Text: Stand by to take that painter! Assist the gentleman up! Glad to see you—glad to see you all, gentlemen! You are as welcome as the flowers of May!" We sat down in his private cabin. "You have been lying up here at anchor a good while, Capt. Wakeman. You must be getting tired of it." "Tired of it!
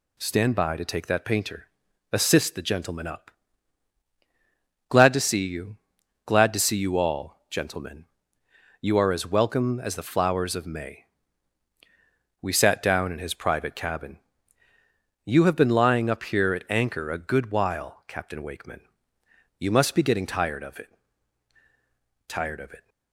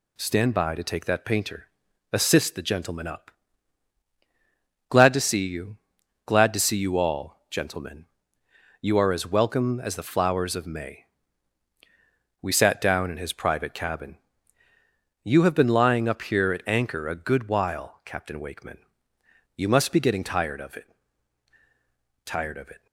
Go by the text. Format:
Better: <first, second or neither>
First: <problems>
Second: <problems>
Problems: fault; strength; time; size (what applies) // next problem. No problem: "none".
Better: neither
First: none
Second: none